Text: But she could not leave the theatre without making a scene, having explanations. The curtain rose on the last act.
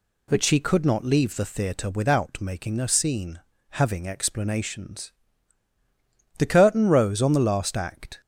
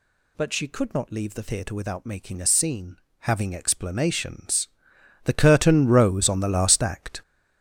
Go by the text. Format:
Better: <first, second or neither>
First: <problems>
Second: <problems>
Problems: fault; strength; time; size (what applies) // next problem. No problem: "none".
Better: first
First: none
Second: gets louder; strong; throughout; 11 dB